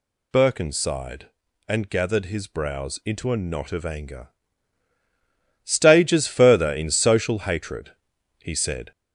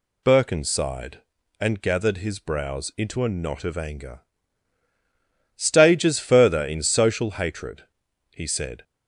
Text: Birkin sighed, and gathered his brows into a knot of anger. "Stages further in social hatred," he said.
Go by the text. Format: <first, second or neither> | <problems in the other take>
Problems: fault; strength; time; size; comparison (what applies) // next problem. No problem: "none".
second | gets louder; throughout; 3.5 dB